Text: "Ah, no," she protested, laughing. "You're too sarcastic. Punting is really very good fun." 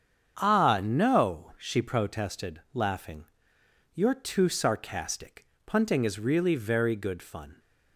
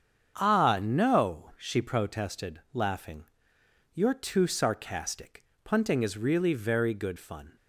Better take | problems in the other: neither | starts louder than the rest; strong; the same in both

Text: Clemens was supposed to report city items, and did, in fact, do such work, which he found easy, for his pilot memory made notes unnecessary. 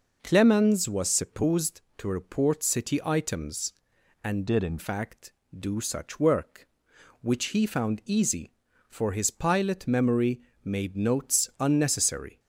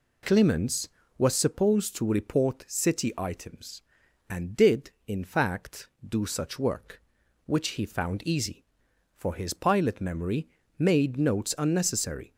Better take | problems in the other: second | changes voice from "did" to "in"; from 4.4 to 4.7 s; 0.3 s long // pauses between "memory" and "made"; slight; at 10.4 s; 0.22 s long; slight in the second

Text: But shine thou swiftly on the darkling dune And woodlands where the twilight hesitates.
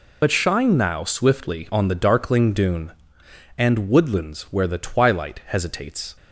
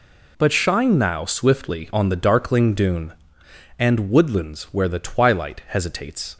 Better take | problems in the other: second | loses the start of "But"; at 0.2 s; 65 ms

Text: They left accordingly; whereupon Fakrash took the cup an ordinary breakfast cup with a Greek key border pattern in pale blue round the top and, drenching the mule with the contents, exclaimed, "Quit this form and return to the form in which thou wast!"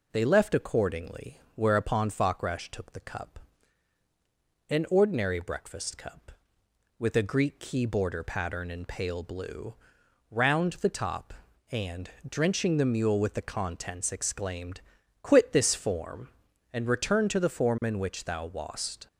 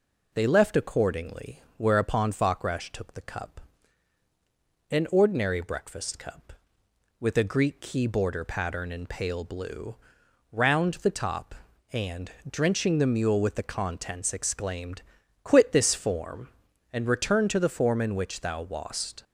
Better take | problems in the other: neither | pauses between "cup" and "an"; strong; the same in both // pauses between "blue" and "round"; noticeable; the same in both

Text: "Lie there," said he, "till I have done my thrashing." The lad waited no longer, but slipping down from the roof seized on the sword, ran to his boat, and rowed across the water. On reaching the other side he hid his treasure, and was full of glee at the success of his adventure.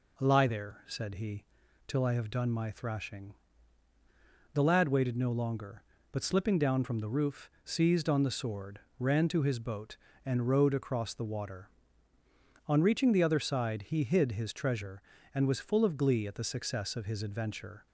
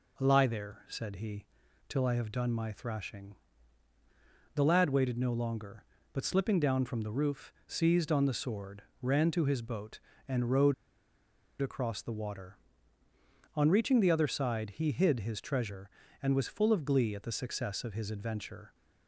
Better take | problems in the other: first | pauses between "roof" and "seized"; slight; at 7.5 s; 0.16 s long; slight in the first // pauses between "rowed" and "across"; noticeable; at 10.7 s; 0.88 s long

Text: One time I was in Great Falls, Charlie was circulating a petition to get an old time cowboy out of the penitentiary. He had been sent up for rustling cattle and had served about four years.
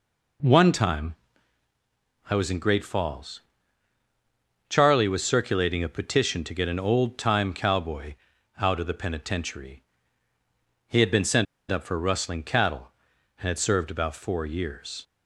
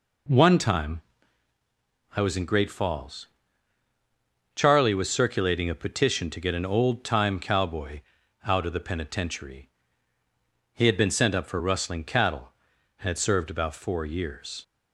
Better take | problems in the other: second | pauses between "time" and "I"; at 1.1 s; 1.1 s long; also in the second // pauses between "cowboy" and "out"; at 8.1 s; 0.44 s long; also in the second // pauses between "sent" and "up"; slight; at 11.4 s; 0.25 s long

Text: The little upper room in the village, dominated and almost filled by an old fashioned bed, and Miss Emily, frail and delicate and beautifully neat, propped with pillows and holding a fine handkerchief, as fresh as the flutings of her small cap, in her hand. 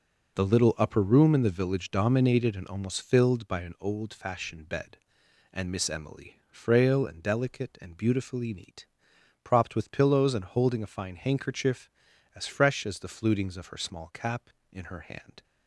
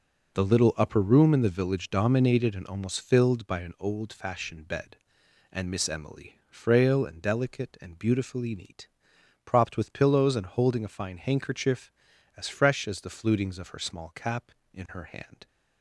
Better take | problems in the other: neither | none

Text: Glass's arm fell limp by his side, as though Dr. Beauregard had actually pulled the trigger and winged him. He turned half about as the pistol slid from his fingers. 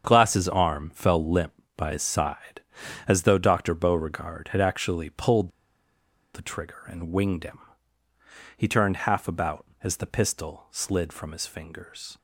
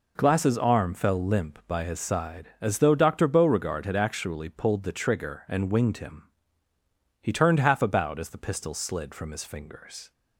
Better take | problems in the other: second | starts louder than the rest; strong; until 1.0 s; 7.5 dB // pauses between "pulled" and "the"; noticeable; at 5.4 s; 0.84 s long

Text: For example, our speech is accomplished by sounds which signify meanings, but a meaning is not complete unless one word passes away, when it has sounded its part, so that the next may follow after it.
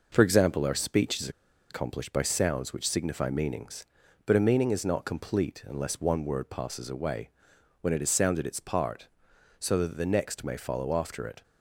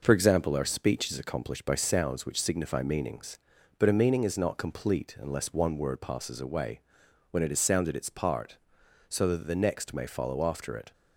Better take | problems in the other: second | pauses between "is" and "accomplished"; at 1.2 s; 0.40 s long

